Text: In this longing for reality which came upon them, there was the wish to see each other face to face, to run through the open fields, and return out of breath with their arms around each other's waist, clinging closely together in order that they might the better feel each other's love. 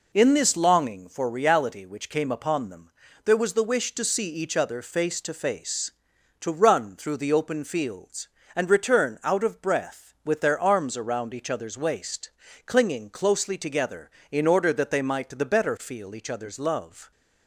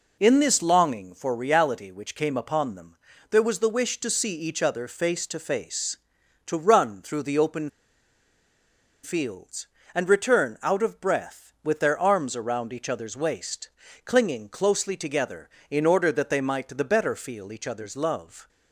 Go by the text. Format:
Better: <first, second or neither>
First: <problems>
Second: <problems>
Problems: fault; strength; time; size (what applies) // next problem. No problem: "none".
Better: first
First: none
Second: pauses between "open" and "fields"; strong; at 7.6 s; 1.3 s long